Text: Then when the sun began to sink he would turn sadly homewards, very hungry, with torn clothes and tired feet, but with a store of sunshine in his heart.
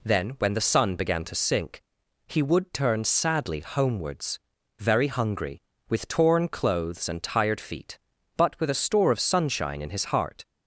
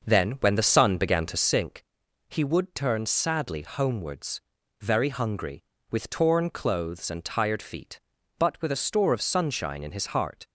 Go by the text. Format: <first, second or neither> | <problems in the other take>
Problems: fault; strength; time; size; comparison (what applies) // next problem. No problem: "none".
first | starts louder than the rest; until 1.8 s; 6 dB // pauses between "sink" and "he"; noticeable; at 1.8 s; 0.46 s long; noticeable in the first